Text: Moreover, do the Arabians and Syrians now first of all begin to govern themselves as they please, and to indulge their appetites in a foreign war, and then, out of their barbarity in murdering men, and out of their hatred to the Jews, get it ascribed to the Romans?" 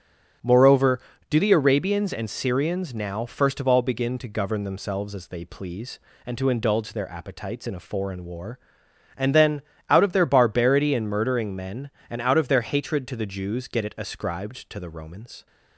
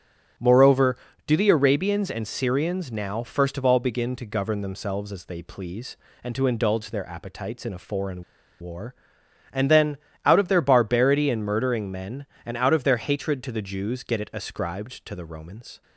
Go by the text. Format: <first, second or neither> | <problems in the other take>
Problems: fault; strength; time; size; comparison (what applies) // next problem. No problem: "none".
first | starts louder than the rest; strong; until 1.6 s; 8 dB; strong in the first // pauses between "foreign" and "war"; at 8.2 s; 0.37 s long